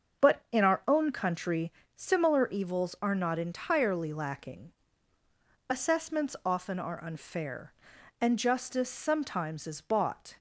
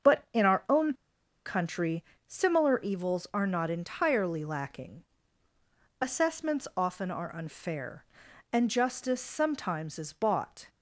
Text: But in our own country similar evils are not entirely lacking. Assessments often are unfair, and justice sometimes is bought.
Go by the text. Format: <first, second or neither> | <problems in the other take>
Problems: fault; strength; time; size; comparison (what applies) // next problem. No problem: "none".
first | starts louder than the rest; until 1.7 s; 7 dB; also in the first // pauses between "own" and "country"; noticeable; at 0.9 s; 0.52 s long // pauses between "country" and "similar"; slight; at 2.0 s; 0.24 s long; slight in the first